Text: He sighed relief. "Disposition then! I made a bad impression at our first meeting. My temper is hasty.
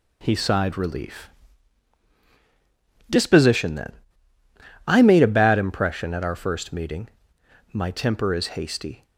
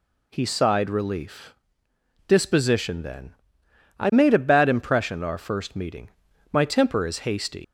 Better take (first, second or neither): first